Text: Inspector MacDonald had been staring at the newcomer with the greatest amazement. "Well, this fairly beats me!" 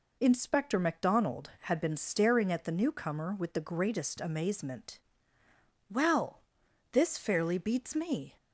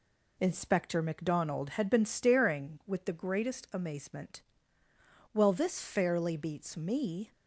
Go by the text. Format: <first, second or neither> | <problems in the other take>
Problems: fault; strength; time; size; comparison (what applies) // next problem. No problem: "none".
first | skips "at the newcomer"; at 2.8 s